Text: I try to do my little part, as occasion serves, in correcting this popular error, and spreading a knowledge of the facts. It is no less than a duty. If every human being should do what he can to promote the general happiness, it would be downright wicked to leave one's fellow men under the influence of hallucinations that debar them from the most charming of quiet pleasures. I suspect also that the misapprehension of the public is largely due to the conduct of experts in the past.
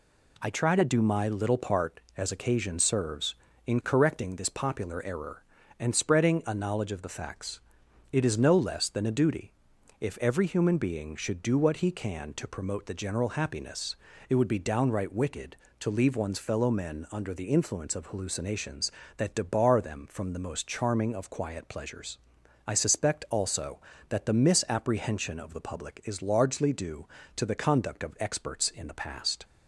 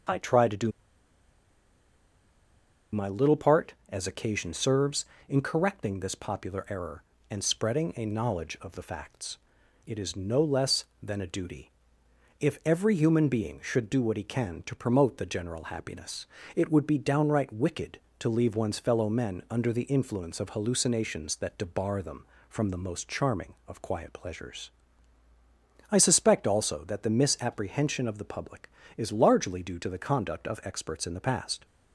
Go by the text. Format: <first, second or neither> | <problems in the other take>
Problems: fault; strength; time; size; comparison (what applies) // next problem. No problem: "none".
first | pauses between "do" and "my"; strong; at 0.7 s; 2.2 s long